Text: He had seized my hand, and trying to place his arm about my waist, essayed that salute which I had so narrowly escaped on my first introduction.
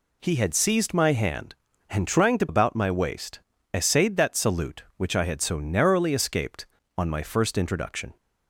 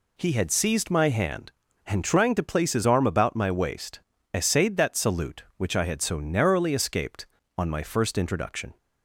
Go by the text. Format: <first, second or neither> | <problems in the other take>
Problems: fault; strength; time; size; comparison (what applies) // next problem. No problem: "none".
second | skips "place his arm"; at 2.4 s